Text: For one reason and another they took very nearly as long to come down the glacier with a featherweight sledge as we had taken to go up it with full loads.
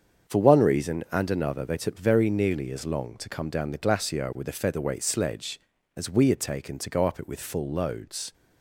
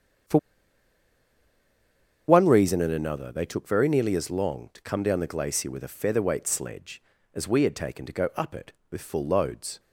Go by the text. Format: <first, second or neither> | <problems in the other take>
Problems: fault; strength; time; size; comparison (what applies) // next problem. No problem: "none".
first | starts louder than the rest; strong; until 3.1 s; 8 dB; strong in the first // pauses between "For" and "one"; strong; at 0.3 s; 1.8 s long